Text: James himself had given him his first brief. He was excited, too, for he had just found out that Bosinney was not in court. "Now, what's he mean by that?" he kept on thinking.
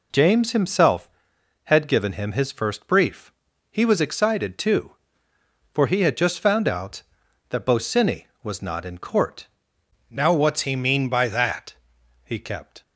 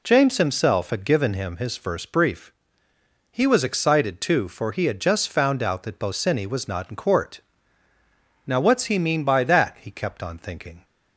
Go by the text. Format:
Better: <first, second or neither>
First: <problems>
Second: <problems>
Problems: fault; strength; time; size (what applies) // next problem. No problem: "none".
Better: second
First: stops before "on thinking"; at 12.8 s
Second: none